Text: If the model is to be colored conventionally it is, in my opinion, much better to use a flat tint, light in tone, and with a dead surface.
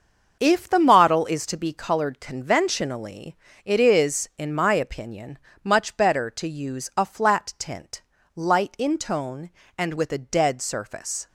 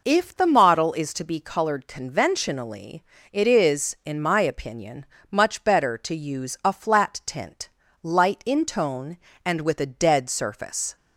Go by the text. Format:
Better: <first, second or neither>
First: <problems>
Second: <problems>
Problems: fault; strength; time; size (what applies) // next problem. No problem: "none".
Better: second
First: gets quieter; strong; throughout; 8.5 dB // pauses between "conventionally" and "it"; slight; at 3.3 s; 0.28 s long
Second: pauses between "conventionally" and "it"; slight; at 3.0 s; 0.28 s long